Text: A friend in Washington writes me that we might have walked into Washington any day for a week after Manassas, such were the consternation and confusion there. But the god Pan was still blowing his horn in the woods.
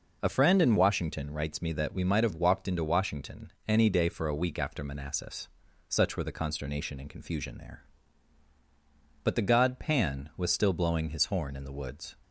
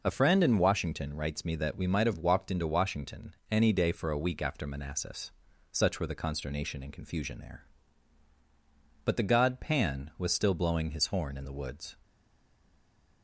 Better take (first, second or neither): first